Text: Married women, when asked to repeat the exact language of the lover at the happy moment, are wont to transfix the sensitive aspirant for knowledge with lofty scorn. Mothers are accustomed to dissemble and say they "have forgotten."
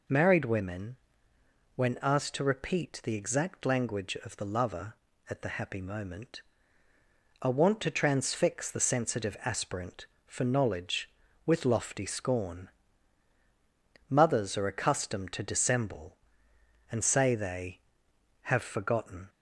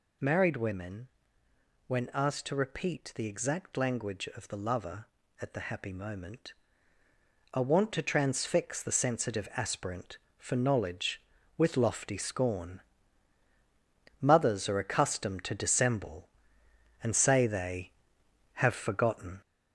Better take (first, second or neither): first